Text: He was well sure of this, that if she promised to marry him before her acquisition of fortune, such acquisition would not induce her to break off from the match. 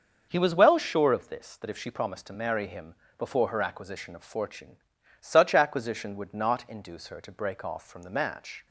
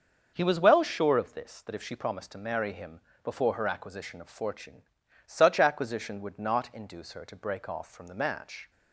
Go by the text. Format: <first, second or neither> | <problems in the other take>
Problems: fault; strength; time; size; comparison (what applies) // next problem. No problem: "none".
neither | starts louder than the rest; the same in both // pauses between "him" and "before"; slight; the same in both